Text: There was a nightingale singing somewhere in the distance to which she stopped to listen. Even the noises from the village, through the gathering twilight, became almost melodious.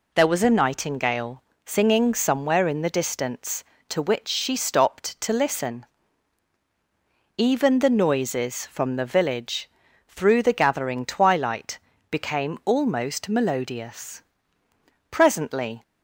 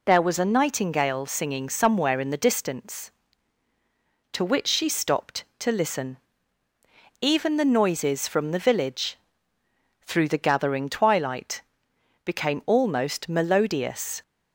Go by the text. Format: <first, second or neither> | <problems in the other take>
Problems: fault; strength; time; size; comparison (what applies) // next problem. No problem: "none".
second | pauses between "nightingale" and "singing"; slight; at 1.4 s; 0.22 s long // goes on to say "Presently"; noticeable; from 15.1 s on; 0.72 s long